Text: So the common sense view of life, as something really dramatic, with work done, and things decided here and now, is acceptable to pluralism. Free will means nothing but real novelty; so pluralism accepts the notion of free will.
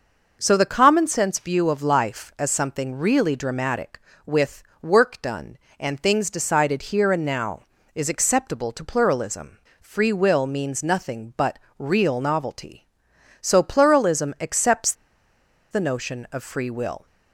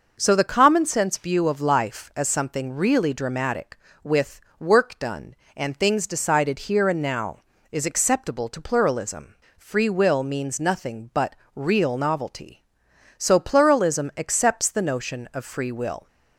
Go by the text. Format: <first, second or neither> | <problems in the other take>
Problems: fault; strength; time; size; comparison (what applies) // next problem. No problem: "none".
second | pauses between "with" and "work"; slight; at 4.6 s; 0.18 s long; slight in the second // pauses between "but" and "real"; slight; at 11.5 s; 0.18 s long; slight in the second // pauses between "accepts" and "the"; noticeable; at 14.9 s; 0.78 s long